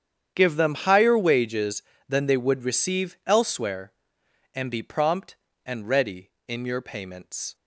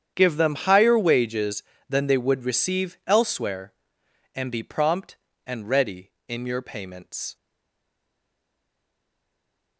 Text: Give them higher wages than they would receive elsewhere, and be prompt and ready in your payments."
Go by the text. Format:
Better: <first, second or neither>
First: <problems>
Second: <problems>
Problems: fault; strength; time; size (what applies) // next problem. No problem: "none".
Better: first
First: starts louder than the rest; strong; until 1.3 s; 8.5 dB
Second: starts louder than the rest; strong; until 1.1 s; 8.5 dB // stays silent after the last word; from 7.3 s on; 2.4 s long